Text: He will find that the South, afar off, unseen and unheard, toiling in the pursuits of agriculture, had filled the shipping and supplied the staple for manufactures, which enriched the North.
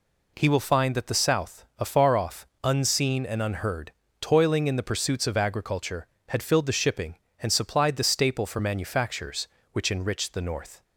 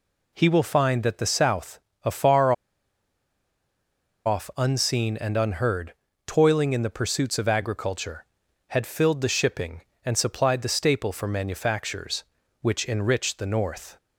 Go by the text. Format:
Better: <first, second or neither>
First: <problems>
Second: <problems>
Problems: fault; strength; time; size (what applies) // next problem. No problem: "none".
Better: first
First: none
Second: pauses between "afar" and "off"; strong; at 2.5 s; 1.7 s long